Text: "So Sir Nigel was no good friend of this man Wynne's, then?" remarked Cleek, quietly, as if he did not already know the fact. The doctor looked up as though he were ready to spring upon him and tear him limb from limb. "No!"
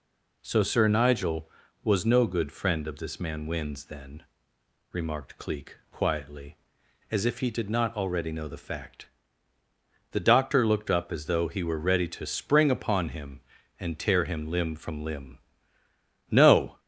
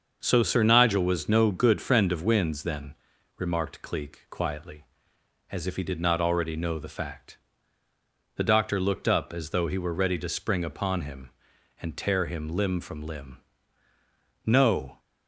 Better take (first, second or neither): first